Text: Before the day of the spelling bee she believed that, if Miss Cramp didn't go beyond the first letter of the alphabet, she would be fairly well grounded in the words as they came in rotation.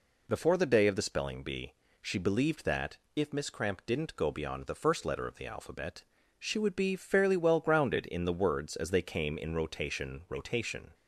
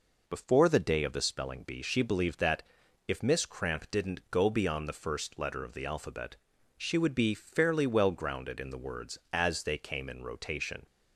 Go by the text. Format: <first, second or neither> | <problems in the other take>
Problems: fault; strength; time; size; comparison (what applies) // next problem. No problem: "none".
second | pauses between "bee" and "she"; slight; at 1.7 s; 0.26 s long // says "rotation" twice; at 10.2 s